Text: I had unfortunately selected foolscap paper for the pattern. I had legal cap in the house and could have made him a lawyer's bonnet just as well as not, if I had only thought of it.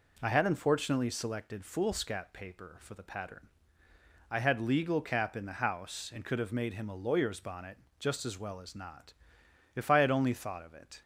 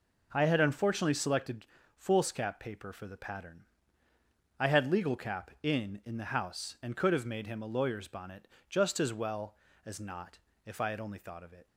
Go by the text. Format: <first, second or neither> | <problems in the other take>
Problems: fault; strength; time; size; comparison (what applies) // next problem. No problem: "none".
first | pauses between "selected" and "foolscap"; slight; at 1.6 s; 0.32 s long // says "in" twice; at 6.0 s // pauses between "bonnet" and "just"; slight; at 8.4 s; 0.22 s long; slight in the first